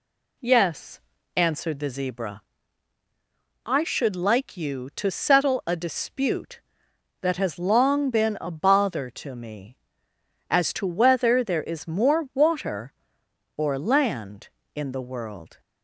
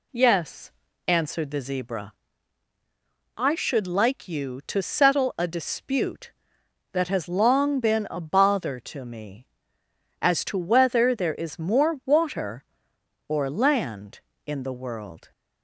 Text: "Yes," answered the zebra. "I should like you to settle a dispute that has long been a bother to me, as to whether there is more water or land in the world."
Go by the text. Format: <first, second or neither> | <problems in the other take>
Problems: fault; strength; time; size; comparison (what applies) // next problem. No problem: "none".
neither | none